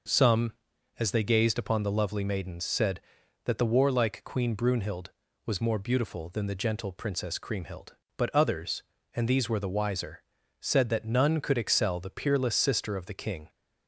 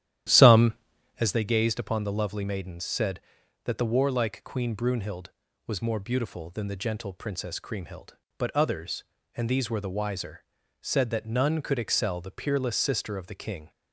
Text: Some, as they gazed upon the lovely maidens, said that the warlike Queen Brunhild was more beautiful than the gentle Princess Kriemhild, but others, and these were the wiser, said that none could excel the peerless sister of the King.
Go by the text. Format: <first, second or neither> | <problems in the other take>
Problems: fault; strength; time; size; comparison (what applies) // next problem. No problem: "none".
first | starts louder than the rest; strong; until 1.4 s; 11.5 dB